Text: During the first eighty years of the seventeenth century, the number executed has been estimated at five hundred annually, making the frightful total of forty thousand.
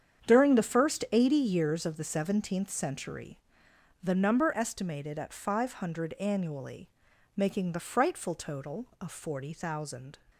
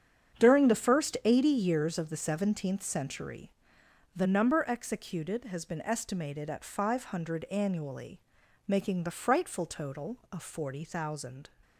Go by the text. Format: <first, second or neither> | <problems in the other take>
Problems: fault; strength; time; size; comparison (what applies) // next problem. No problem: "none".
second | starts louder than the rest; strong; until 1.3 s; 8 dB; strong in the second // skips "executed has been"; at 4.5 s